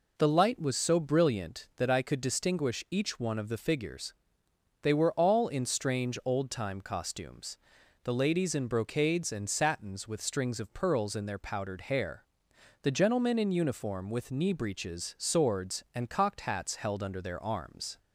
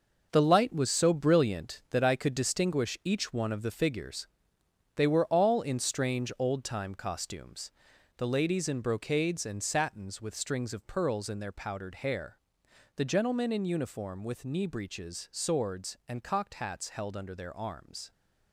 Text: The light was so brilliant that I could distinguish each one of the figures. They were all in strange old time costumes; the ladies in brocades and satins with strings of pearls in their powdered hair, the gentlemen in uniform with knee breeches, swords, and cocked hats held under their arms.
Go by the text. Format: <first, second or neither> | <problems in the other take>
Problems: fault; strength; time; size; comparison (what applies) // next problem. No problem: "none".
first | gets quieter; strong; throughout; 9 dB